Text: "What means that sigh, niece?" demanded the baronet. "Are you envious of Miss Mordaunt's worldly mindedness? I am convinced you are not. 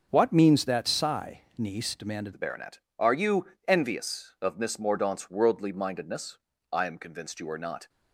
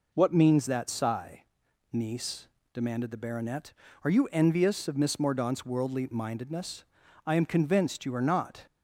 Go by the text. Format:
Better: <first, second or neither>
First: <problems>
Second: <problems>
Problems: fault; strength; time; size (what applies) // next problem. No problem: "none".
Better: second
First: starts louder than the rest; until 1.1 s; 6.5 dB // changes voice at "the"; from 2.3 s on; 5.5 s long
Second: none